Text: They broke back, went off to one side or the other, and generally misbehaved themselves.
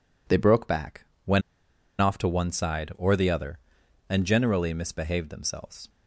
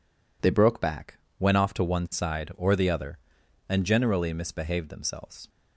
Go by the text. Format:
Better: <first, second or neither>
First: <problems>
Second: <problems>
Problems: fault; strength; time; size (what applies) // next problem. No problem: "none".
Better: second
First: pauses between "went" and "off"; noticeable; at 1.4 s; 0.59 s long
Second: none